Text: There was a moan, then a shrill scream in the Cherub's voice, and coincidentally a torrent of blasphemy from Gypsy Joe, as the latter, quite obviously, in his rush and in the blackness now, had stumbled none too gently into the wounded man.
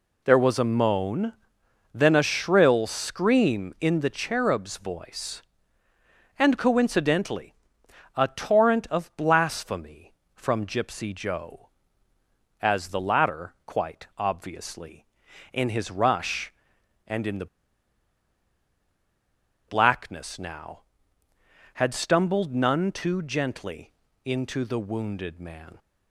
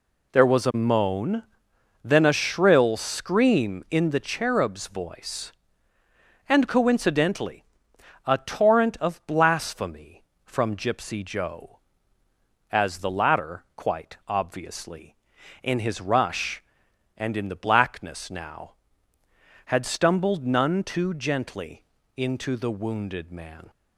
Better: second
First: pauses between "coincidentally" and "a"; noticeable; at 7.5 s; 0.62 s long // pauses between "the" and "blackness"; strong; at 17.4 s; 2.2 s long // pauses between "gently" and "into"; slight; at 23.9 s; 0.34 s long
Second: pauses between "coincidentally" and "a"; noticeable; at 7.6 s; 0.62 s long // pauses between "gently" and "into"; slight; at 21.8 s; 0.34 s long

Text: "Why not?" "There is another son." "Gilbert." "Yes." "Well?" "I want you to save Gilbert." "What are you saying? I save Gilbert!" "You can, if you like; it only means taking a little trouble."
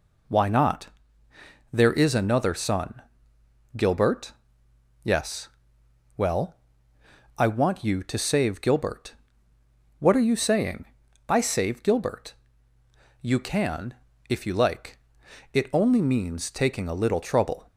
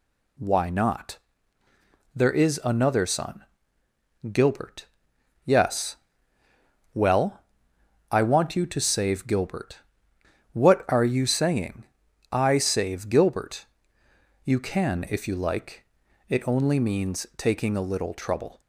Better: neither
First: none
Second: none

